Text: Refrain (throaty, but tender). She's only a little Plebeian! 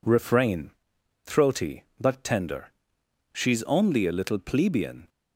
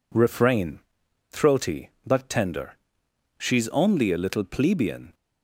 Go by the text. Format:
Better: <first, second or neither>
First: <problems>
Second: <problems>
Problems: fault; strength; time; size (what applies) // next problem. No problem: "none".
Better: neither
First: none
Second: none